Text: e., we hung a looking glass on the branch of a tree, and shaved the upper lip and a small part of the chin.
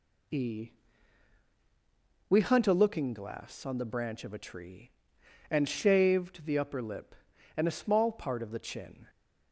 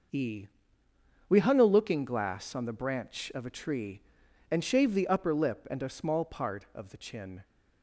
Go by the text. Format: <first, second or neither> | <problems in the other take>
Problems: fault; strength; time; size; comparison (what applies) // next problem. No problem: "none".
second | says "hunt" for "hung"; at 2.4 s